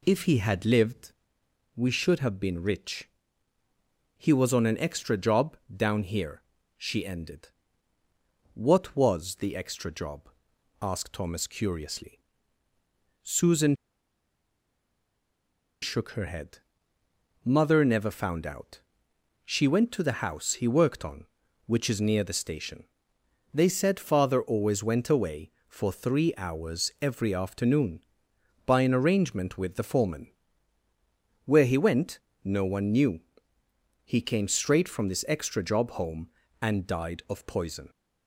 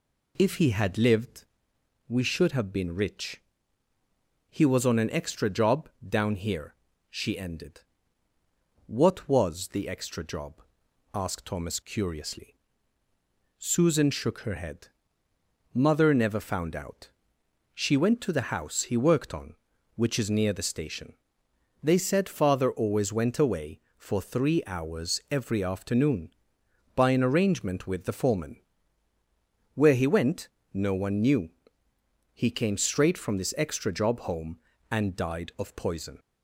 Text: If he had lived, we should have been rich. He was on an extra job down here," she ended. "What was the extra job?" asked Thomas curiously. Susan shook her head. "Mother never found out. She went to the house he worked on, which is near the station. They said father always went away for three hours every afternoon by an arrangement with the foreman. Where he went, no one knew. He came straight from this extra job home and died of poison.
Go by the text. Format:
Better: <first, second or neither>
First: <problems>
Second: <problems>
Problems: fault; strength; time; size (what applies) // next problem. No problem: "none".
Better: second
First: pauses between "job" and "down"; slight; at 5.5 s; 0.18 s long // pauses between "Susan" and "shook"; strong; at 13.7 s; 2.0 s long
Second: pauses between "job" and "down"; slight; at 5.8 s; 0.18 s long